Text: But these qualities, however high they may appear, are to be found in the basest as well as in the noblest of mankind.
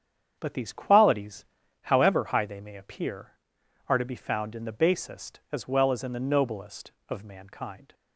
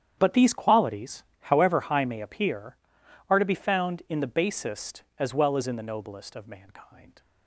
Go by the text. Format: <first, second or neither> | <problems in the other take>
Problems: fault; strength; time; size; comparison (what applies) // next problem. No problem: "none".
first | starts louder than the rest; strong; until 1.1 s; 9 dB; strong in the first // skips "they"; at 2.0 s